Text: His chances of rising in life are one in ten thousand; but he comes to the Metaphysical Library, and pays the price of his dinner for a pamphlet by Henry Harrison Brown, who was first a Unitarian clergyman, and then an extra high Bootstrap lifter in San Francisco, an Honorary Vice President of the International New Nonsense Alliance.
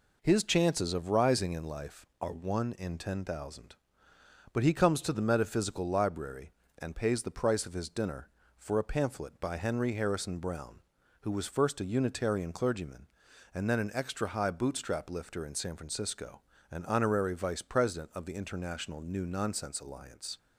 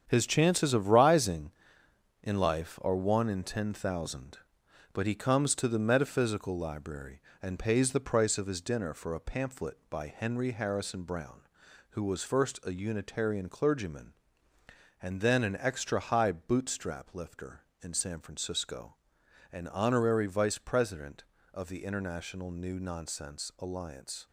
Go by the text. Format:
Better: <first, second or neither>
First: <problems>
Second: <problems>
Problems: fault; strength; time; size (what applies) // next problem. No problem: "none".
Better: first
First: none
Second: gets quieter; strong; throughout; 8 dB